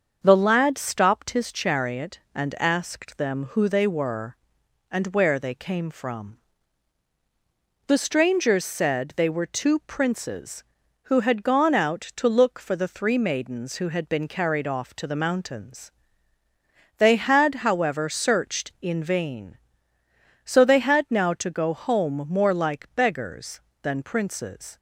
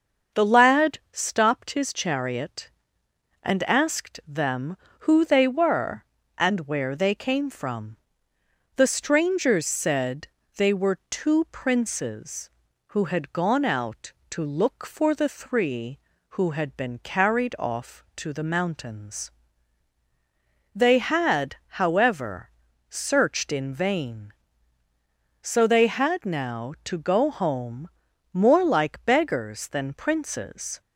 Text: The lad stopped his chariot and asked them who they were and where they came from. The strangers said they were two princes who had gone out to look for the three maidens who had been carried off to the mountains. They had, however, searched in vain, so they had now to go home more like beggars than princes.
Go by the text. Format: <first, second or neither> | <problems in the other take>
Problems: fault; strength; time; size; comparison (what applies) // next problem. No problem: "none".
first | starts louder than the rest; until 1.4 s; 6.5 dB; also in the first // pauses between "said" and "they"; slight; at 10.2 s; 0.28 s long // skips "maidens"; at 16.1 s // pauses between "home" and "more"; at 27.9 s; 0.44 s long